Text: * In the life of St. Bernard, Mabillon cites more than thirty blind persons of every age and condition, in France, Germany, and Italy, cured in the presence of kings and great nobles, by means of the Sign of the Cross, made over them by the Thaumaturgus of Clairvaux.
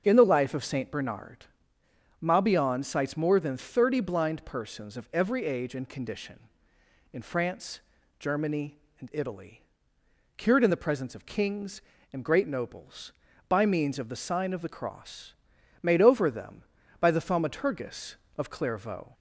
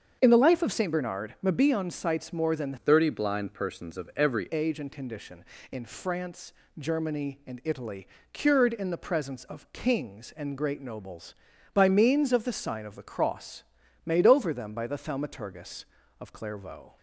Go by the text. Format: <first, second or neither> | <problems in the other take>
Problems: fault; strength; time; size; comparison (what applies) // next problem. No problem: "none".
first | starts louder than the rest; until 1.2 s; 7 dB; also in the first // changes voice from "thirty" to "every"; from 2.7 to 4.4 s; 1.7 s long